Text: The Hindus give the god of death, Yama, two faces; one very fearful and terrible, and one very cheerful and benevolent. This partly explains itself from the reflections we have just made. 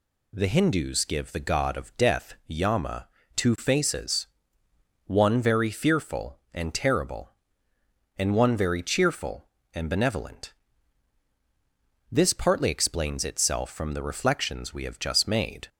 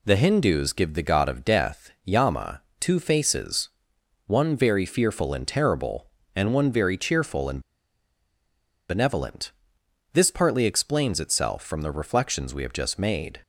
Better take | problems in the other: first | pauses between "and" and "benevolent"; strong; at 7.6 s; 1.2 s long

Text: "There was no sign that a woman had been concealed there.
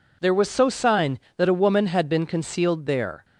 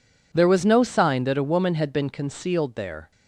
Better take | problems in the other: second | says "so" for "no"; at 0.4 s

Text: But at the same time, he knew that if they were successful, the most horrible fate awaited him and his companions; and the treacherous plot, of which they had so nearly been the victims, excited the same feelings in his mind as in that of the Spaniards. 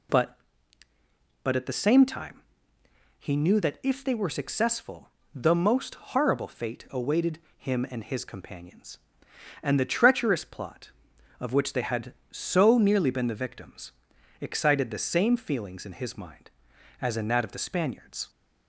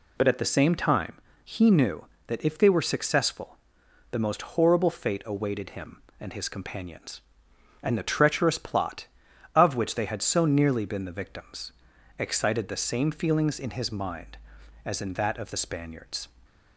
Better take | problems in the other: second | says "But" twice; at 1.4 s // pauses between "awaited" and "him"; slight; at 7.3 s; 0.18 s long

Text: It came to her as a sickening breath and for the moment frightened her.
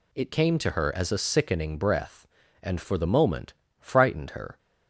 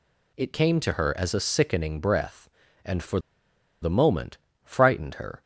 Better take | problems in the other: first | pauses between "for" and "the"; noticeable; at 3.1 s; 0.62 s long // pauses between "moment" and "frightened"; slight; at 4.3 s; 0.26 s long; slight in the first

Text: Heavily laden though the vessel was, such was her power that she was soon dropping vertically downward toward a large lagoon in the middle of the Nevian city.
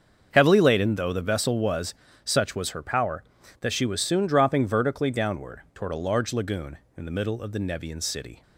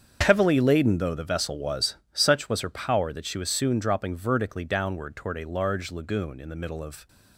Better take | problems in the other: first | starts louder than the rest; strong; until 1.2 s; 7 dB; also in the first // stops before "the Nevian city"; at 7.0 s

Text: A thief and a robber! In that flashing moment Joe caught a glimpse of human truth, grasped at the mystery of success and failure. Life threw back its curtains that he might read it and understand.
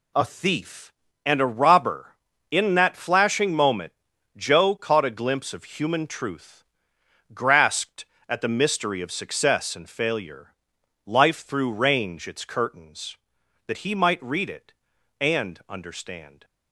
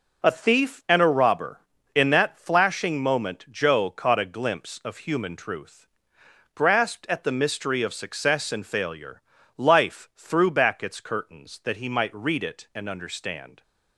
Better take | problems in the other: second | pauses between "moment" and "Joe"; at 3.9 s; 0.44 s long // says "range" for "back"; at 11.7 s

